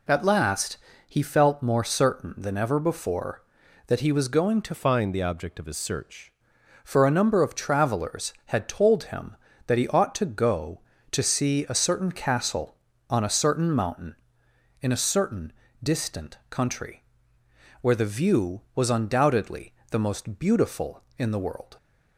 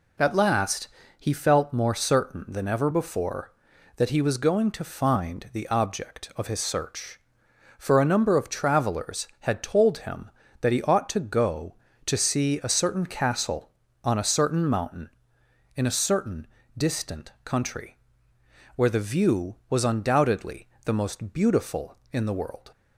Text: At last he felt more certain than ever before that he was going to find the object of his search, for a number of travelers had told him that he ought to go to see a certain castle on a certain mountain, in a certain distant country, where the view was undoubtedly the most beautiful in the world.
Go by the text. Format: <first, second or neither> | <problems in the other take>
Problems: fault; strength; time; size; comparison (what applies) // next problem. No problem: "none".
second | pauses between "last" and "he"; slight; at 0.7 s; 0.30 s long; slight in the second // changes voice from "find" to "search"; from 4.7 to 6.3 s; 1.6 s long // pauses between "certain" and "distant"; slight; at 15.5 s; 0.30 s long; slight in the second // pauses between "undoubtedly" and "the"; slight; at 19.7 s; 0.18 s long; slight in the second